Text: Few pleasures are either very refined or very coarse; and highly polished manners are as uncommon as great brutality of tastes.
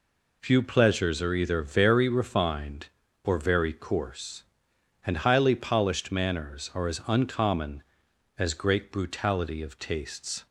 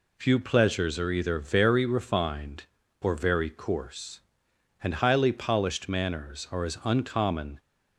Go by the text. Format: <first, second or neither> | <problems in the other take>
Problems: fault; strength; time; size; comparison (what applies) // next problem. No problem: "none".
first | stops before "as great brutality of tastes"; at 7.5 s